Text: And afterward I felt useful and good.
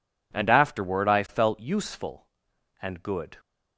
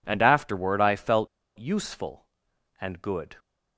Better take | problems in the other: first | pauses between "felt" and "useful"; slight; at 1.2 s; 0.31 s long

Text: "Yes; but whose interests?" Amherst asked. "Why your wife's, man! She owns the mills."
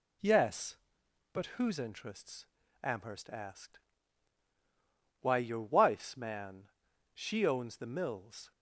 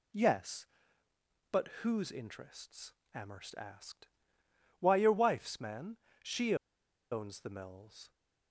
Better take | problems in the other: first | pauses between "but" and "whose"; slight; at 1.6 s; 0.16 s long // pauses between "She" and "owns"; noticeable; at 6.5 s; 0.56 s long

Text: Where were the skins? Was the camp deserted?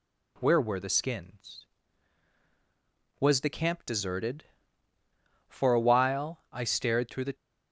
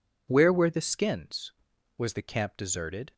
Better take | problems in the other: second | goes on to say "For a while I stared through the"; strong; from 5.4 s on; 1.8 s long

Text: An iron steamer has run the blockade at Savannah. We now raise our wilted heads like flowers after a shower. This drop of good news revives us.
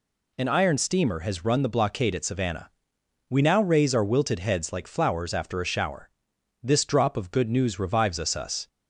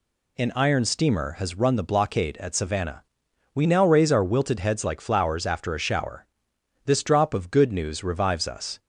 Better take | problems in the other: second | says "us" twice; at 8.3 s

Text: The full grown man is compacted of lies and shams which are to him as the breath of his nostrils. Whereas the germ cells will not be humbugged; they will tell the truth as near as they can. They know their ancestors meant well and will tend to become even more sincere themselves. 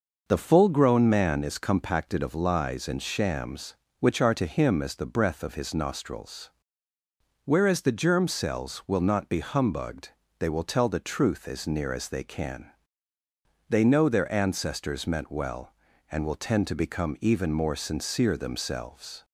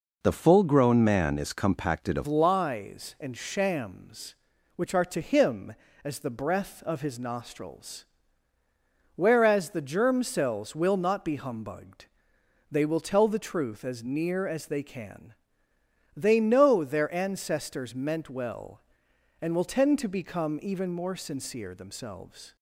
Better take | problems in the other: first | changes voice at "lies"; from 2.2 s on; 20.3 s long

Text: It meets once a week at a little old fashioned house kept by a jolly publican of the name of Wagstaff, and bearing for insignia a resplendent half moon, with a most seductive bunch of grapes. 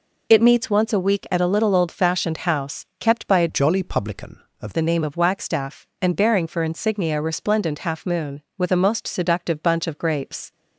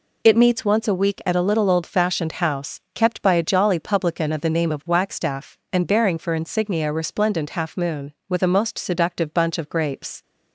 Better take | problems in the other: second | changes voice from "jolly" to "of"; from 3.4 to 4.7 s; 1.3 s long

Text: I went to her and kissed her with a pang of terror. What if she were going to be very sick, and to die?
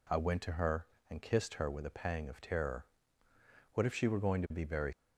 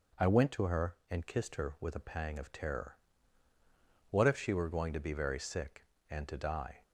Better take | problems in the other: second | stops before "sick and to die"; at 4.9 s

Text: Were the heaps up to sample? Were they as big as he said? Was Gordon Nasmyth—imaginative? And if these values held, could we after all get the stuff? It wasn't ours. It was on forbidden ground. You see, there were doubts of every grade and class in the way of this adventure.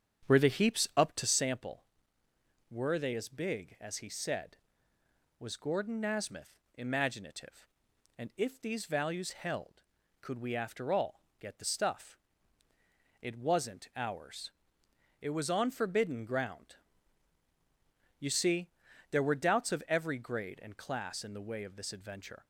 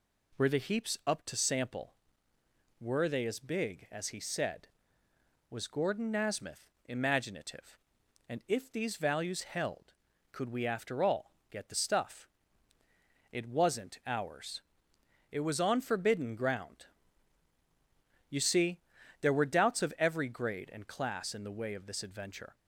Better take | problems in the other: second | starts louder than the rest; strong; until 1.5 s; 8 dB // pauses between "all" and "get"; slight; at 11.2 s; 0.20 s long; slight in the second

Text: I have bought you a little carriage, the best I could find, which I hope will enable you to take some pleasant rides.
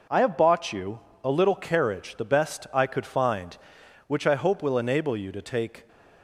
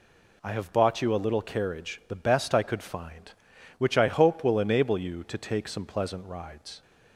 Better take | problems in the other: second | pauses between "you" and "a"; slight; at 0.9 s; 0.22 s long // stops before "some pleasant rides"; at 5.8 s

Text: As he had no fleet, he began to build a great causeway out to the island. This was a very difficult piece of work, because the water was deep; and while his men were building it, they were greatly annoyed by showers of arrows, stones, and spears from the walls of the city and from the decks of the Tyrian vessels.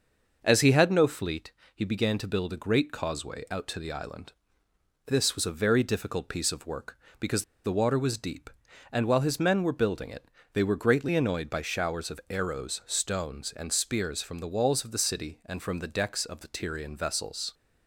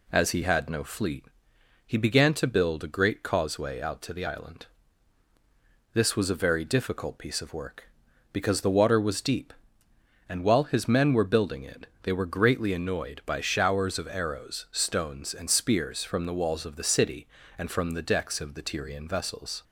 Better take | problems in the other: second | starts louder than the rest; noticeable; until 1.4 s; 6 dB // pauses between "because" and "the"; slight; at 7.4 s; 0.20 s long

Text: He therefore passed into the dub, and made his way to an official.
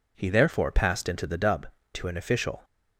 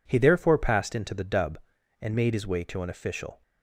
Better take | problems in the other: second | skips "and made his way"; at 1.7 s

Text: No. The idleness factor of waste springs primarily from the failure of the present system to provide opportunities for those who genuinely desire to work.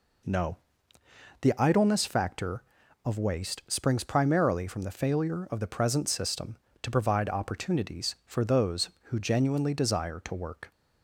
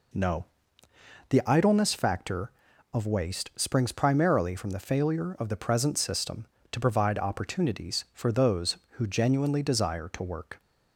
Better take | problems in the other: neither | none

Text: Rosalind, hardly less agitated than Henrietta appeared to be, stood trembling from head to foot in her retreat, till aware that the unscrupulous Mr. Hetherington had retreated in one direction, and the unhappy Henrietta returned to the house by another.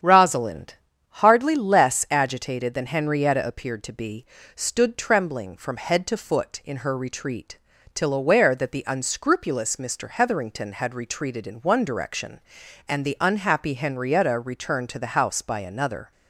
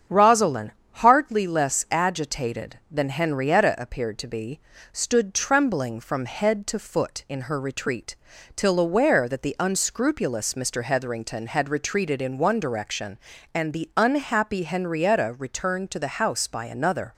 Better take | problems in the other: neither | starts louder than the rest; strong; the same in both

